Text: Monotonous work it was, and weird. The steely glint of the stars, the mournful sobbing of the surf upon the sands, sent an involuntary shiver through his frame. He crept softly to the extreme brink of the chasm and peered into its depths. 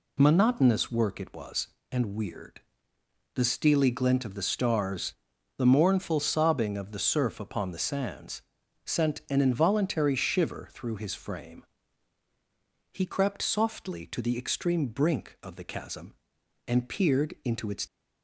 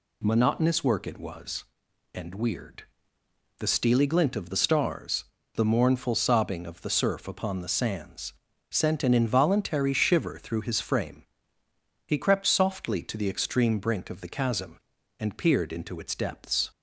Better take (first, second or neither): second